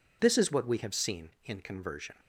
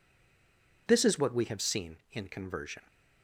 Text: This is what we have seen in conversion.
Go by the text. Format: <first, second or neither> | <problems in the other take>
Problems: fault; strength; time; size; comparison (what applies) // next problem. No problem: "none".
first | stays silent before the first word; slight; until 0.8 s; 0.8 s long